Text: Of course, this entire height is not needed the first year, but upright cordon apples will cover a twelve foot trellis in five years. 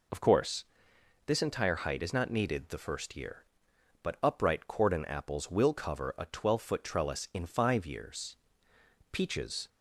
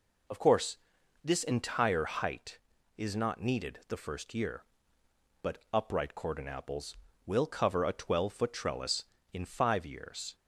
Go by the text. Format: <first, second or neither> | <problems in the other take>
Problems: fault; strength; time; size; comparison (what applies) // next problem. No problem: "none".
second | goes on to say "Peaches"; from 9.1 s on; 0.56 s long